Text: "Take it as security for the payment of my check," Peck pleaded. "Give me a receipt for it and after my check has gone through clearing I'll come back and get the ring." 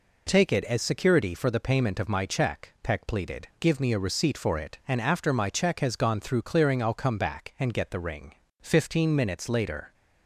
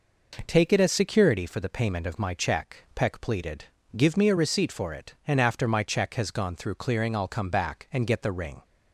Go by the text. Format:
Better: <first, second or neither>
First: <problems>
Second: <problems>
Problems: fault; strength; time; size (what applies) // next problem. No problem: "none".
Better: second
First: goes on to say "Fifteen minutes later"; from 8.5 s on; 1.3 s long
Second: none